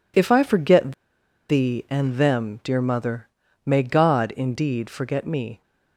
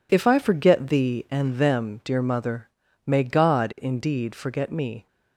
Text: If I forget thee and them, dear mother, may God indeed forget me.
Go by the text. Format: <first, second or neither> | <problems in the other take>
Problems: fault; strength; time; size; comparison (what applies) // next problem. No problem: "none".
second | pauses between "forget" and "thee"; noticeable; at 0.9 s; 0.56 s long